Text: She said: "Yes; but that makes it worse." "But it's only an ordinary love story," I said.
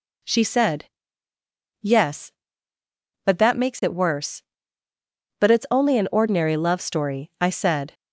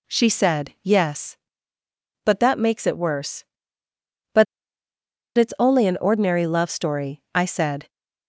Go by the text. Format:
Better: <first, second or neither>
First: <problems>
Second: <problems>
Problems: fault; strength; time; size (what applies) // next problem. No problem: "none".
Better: first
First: none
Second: pauses between "But" and "it's"; noticeable; at 4.4 s; 0.91 s long